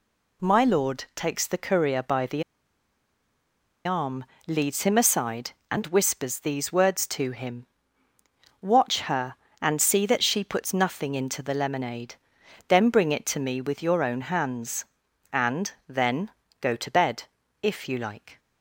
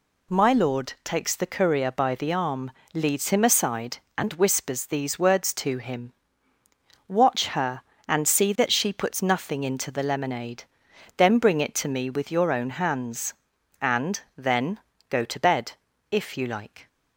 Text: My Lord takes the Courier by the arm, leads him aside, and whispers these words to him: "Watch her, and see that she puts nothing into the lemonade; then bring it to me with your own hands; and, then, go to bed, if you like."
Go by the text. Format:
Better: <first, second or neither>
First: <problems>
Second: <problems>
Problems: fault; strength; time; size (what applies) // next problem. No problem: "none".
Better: second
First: pauses between "the" and "arm"; strong; at 2.4 s; 1.4 s long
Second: none